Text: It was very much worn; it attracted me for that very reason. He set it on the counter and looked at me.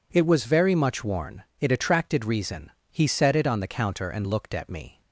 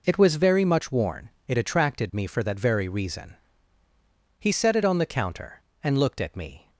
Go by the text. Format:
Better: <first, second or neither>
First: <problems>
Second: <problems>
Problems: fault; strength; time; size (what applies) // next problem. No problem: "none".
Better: second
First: skips "me for that very"; at 2.2 s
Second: none